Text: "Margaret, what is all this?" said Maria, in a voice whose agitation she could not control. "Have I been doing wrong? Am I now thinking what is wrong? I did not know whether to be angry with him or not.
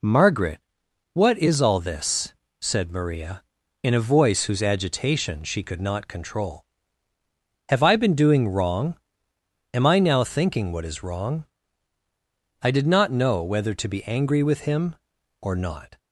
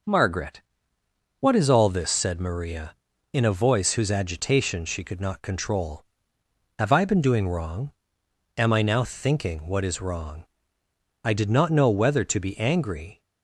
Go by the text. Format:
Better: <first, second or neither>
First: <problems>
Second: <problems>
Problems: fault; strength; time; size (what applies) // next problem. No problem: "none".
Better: first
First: none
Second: stops before "with him or not"; at 13.2 s